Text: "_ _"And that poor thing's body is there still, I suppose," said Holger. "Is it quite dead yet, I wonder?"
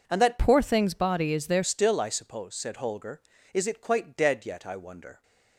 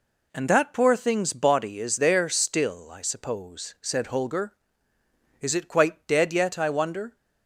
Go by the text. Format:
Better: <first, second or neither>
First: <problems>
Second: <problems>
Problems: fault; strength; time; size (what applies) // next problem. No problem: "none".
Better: second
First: changes voice from "poor" to "there"; from 0.3 to 1.6 s; 1.3 s long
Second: none